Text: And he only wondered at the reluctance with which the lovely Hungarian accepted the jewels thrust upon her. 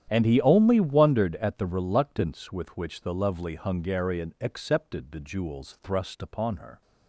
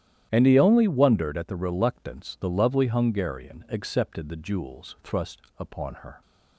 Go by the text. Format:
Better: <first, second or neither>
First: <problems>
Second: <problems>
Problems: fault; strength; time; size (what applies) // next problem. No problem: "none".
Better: first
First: starts louder than the rest; strong; until 1.1 s; 10 dB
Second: starts louder than the rest; strong; until 1.3 s; 11.5 dB // skips "with which"; at 2.3 s // pauses between "thrust" and "upon"; slight; at 5.3 s; 0.18 s long